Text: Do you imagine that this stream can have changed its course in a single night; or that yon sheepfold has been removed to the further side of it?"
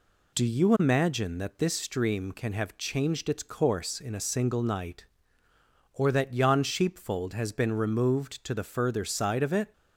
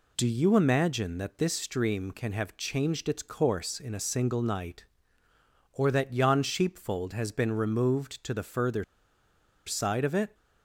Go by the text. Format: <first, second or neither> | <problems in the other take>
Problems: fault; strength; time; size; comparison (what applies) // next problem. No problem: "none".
first | pauses between "further" and "side"; noticeable; at 8.8 s; 0.84 s long